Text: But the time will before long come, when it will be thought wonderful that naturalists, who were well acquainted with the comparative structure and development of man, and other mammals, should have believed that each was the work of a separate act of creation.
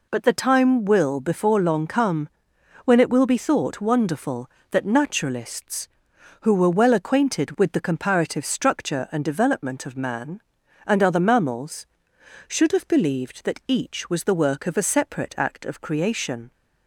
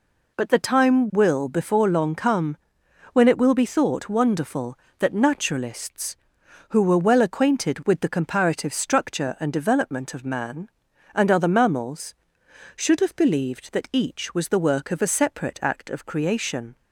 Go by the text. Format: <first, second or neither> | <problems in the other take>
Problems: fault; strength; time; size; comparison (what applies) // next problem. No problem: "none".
neither | none